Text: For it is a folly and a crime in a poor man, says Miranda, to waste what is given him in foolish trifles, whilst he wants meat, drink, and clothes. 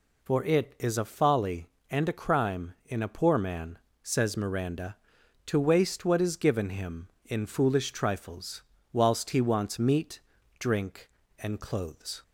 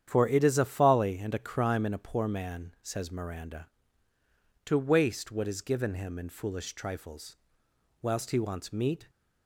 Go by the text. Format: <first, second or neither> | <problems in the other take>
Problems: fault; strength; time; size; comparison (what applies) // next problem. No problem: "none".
first | starts louder than the rest; strong; until 1.1 s; 9.5 dB // stops before "drink and clothes"; at 9.0 s